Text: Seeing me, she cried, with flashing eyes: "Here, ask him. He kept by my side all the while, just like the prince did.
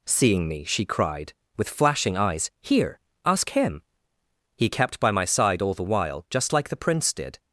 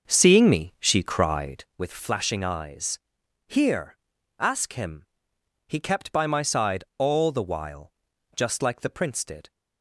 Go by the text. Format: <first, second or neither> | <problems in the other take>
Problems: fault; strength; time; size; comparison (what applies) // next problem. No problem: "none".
first | starts louder than the rest; noticeable; until 1.8 s; 6 dB